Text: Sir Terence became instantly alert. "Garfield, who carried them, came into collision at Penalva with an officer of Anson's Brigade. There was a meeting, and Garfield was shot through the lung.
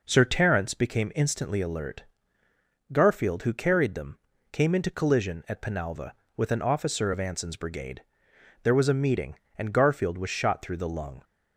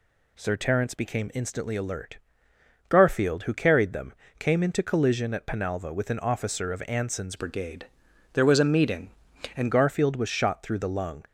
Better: first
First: none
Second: changes voice from "Brigade" to "and"; from 7.3 to 9.7 s; 2.4 s long

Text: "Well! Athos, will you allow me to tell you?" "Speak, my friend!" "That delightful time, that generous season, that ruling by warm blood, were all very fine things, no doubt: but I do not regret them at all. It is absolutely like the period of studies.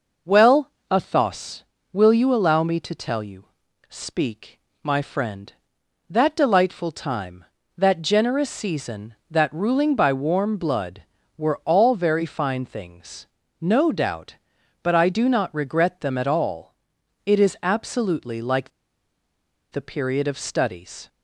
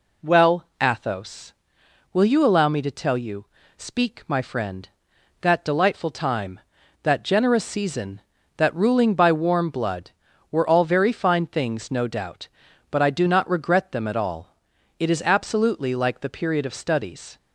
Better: second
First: pauses between "like" and "the"; at 18.6 s; 1.0 s long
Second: none

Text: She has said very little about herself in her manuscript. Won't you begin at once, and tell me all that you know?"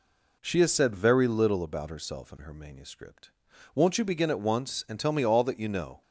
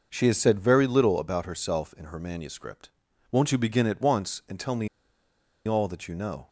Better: first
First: none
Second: pauses between "me" and "all"; noticeable; at 4.8 s; 0.79 s long

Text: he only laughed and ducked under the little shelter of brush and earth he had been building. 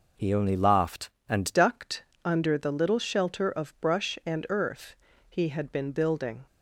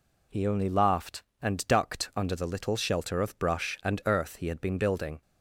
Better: second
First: changes voice at "ducked"; from 1.5 s on; 4.9 s long // pauses between "ducked" and "under"; slight; at 2.0 s; 0.22 s long // pauses between "earth" and "he"; slight; at 4.9 s; 0.34 s long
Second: none

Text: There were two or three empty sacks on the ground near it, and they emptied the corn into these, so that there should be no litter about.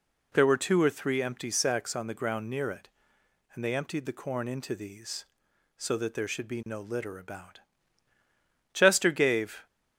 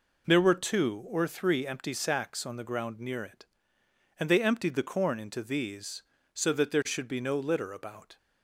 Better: second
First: goes on to say "Chester gave"; noticeable; from 8.7 s on; 0.92 s long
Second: none

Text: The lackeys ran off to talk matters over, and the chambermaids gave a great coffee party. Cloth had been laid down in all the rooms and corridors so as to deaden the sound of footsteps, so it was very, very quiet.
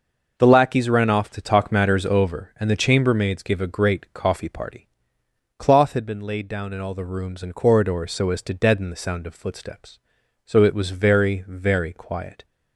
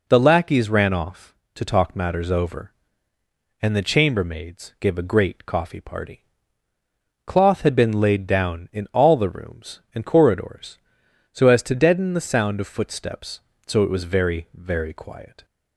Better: neither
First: none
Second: none

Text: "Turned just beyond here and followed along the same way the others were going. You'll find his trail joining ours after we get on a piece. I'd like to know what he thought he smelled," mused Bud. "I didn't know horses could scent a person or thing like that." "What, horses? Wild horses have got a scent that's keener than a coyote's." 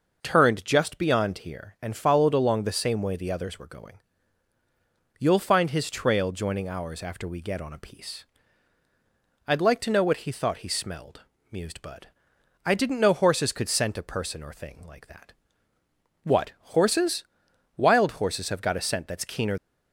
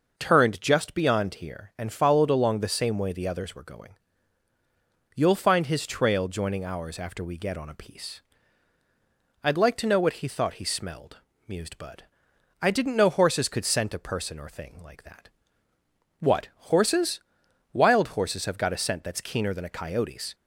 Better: second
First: stops before "than a coyote's"; at 19.5 s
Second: none

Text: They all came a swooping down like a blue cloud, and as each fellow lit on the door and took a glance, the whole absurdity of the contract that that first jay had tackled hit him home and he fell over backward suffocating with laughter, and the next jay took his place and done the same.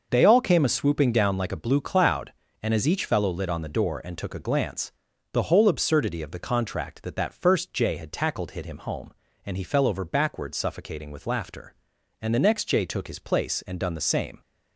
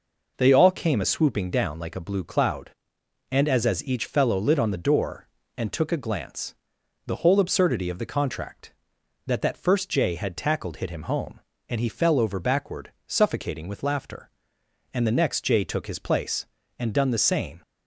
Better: first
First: none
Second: says "as" twice; at 3.6 s

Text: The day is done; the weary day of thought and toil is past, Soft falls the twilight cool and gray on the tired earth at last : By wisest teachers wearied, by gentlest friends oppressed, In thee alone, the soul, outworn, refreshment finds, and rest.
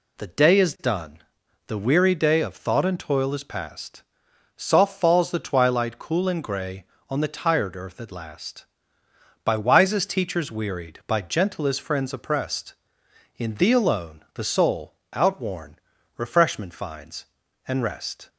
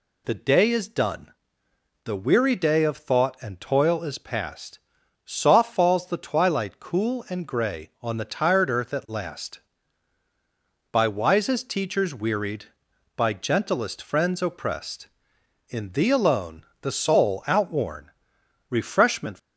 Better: first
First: none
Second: stops before "finds and rest"; at 19.3 s

